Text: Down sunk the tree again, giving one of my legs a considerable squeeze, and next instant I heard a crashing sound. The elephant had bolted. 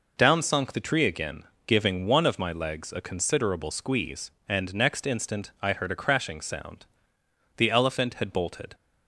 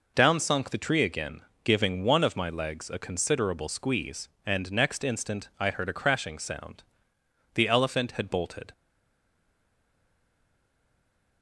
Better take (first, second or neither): first